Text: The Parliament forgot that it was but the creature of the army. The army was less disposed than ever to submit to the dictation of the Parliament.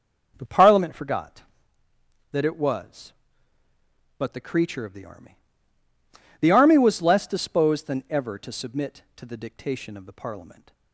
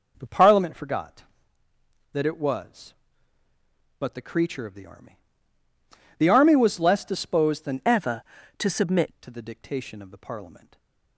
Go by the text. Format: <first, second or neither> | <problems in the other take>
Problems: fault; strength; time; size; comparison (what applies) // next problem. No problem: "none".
first | changes voice from "ever" to "submit"; from 7.8 to 9.1 s; 1.3 s long // stays silent after the last word; slight; from 10.6 s on; 0.5 s long